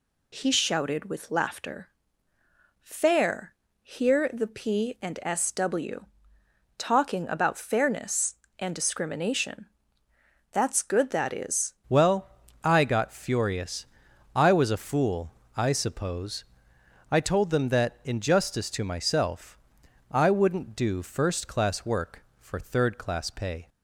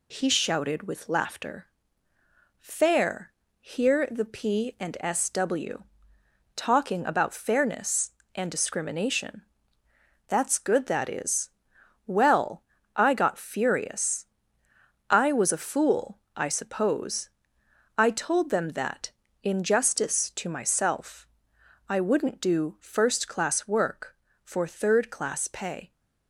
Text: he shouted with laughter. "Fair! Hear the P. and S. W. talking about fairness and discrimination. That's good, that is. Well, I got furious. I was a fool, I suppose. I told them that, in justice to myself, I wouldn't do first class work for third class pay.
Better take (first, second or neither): second